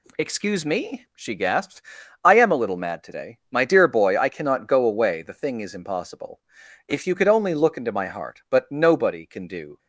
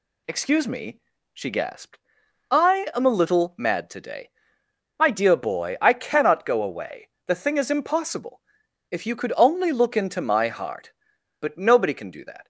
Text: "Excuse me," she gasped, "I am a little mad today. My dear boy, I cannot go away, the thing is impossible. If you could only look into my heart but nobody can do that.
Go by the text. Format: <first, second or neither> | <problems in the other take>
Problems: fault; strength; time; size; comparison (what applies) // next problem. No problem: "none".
second | stops before "that"; at 9.7 s